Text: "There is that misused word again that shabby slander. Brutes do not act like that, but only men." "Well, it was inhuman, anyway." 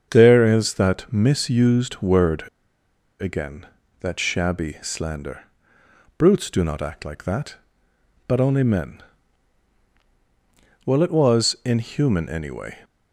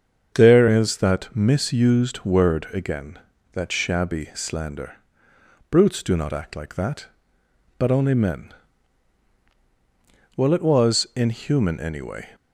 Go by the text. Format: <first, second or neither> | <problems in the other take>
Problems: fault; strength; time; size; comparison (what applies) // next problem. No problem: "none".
second | starts louder than the rest; until 1.1 s; 7 dB; also in the second // pauses between "word" and "again"; noticeable; at 2.4 s; 0.75 s long